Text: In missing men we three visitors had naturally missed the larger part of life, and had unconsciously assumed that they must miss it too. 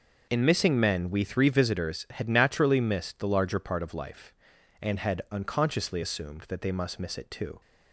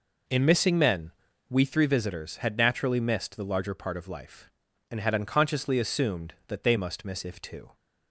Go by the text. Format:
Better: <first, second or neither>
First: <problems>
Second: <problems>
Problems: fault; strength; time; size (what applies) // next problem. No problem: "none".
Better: first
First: none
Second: pauses between "men" and "we"; slight; at 1.1 s; 0.36 s long // says "if" for "it"; at 7.2 s